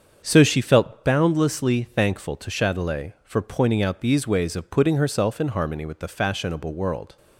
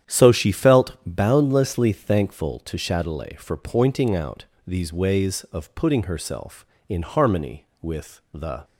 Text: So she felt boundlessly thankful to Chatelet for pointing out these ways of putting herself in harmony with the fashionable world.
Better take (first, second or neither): first